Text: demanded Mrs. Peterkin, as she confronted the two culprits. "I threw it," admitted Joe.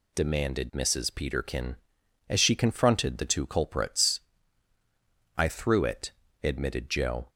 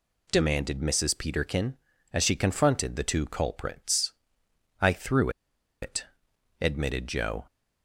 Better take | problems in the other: first | pauses between "threw" and "it"; noticeable; at 5.2 s; 0.52 s long

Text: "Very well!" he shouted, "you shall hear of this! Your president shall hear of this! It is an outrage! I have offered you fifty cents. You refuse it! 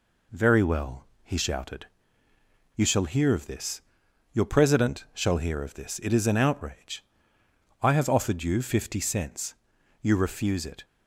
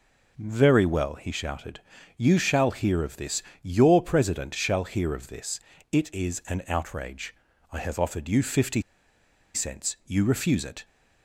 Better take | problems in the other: first | pauses between "fifty" and "cents"; noticeable; at 8.8 s; 0.73 s long

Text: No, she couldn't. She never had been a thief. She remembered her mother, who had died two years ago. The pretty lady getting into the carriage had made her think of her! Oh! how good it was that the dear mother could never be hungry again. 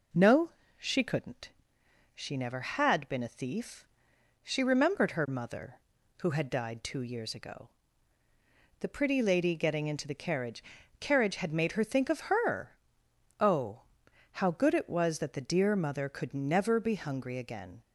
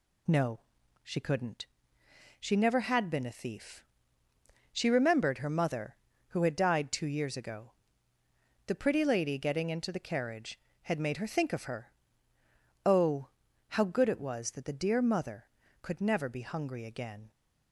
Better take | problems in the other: second | says "carriage" twice; at 10.9 s

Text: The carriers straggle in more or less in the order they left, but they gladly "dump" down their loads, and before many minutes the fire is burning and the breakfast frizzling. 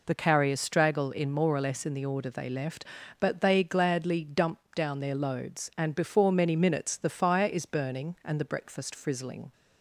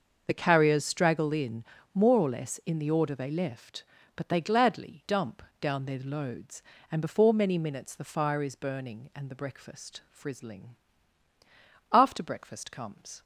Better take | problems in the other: first | starts louder than the rest; until 1.2 s; 6.5 dB // pauses between "in" and "more"; slight; at 1.6 s; 0.30 s long // pauses between "dump" and "down"; slight; at 5.4 s; 0.20 s long; slight in the first // goes on to say "After breakfast comes"; noticeable; from 11.9 s on; 1.3 s long

